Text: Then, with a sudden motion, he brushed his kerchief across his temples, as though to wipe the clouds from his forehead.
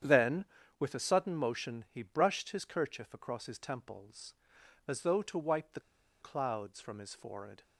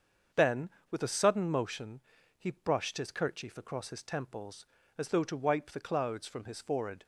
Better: second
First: starts louder than the rest; strong; until 1.3 s; 9 dB // pauses between "the" and "clouds"; at 5.7 s; 0.42 s long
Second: starts louder than the rest; until 1.5 s; 7 dB

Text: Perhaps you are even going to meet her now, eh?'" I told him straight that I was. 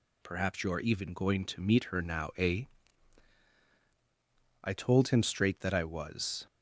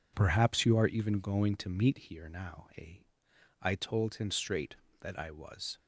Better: first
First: none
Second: says "here" for "her"; at 1.9 s

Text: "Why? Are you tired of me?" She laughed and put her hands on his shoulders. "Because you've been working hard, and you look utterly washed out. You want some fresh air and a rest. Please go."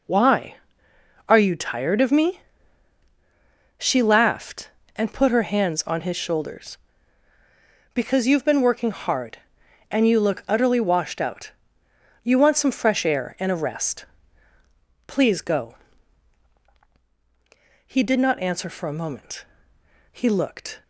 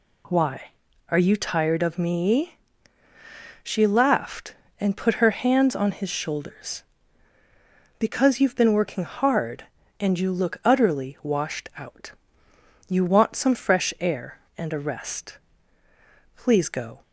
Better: second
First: goes on to say "He did not answer for a moment He looked"; strong; from 17.8 s on; 2.9 s long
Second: none

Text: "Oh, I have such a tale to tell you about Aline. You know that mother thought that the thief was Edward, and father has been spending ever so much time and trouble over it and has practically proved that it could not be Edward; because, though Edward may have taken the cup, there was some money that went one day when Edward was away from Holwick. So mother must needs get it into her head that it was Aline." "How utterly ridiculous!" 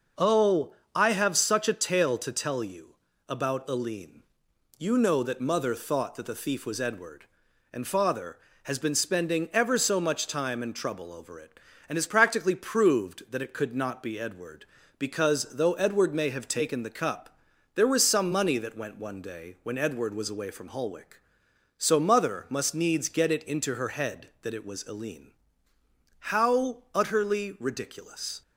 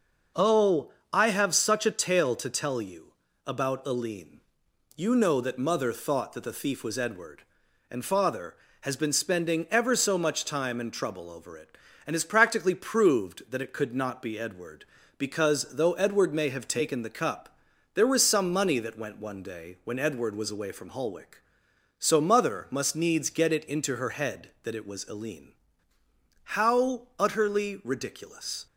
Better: neither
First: pauses between "you" and "about"; slight; at 2.9 s; 0.30 s long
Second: pauses between "you" and "about"; slight; at 3.1 s; 0.30 s long

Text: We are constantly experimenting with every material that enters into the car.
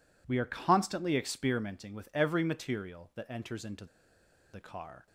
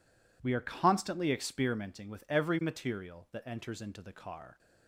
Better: second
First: pauses between "into" and "the"; noticeable; at 3.8 s; 0.67 s long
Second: none

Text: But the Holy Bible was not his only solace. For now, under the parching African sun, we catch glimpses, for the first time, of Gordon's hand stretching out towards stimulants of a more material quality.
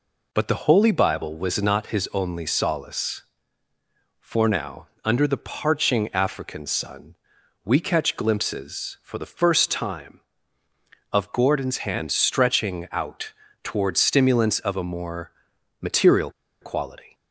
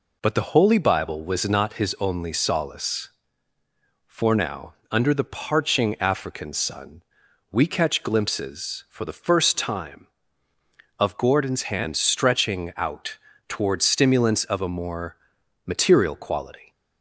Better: second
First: pauses between "out" and "towards"; slight; at 13.3 s; 0.32 s long // pauses between "more" and "material"; noticeable; at 15.3 s; 0.50 s long // pauses between "material" and "quality"; slight; at 16.2 s; 0.31 s long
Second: pauses between "out" and "towards"; slight; at 13.1 s; 0.32 s long // pauses between "more" and "material"; noticeable; at 15.1 s; 0.50 s long

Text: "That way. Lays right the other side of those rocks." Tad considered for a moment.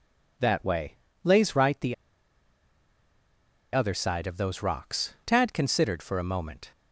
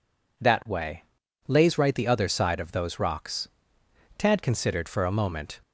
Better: second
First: pauses between "the" and "other"; strong; at 1.9 s; 1.7 s long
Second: none

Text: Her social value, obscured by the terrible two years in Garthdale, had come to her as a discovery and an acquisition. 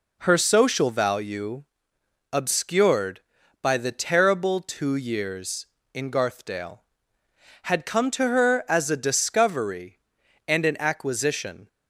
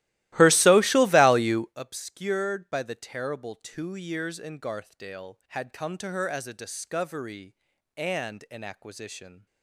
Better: first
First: none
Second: starts louder than the rest; strong; until 1.8 s; 16.5 dB

